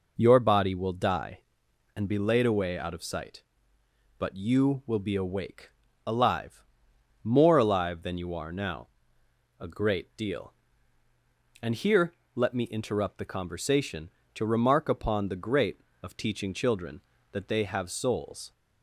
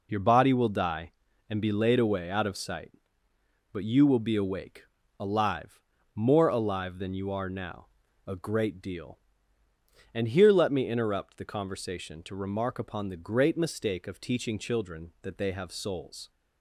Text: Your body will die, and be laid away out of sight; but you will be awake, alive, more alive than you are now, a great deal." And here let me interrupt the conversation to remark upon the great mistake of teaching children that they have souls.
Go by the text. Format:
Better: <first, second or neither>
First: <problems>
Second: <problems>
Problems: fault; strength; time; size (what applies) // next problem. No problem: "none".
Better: second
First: pauses between "here" and "let"; slight; at 12.1 s; 0.20 s long // skips "mistake"; at 15.9 s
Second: none